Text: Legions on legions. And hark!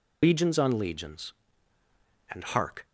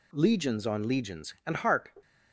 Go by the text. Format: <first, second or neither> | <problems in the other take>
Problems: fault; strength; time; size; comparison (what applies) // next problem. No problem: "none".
second | loses the start of "Legions"; at 0.2 s; 130 ms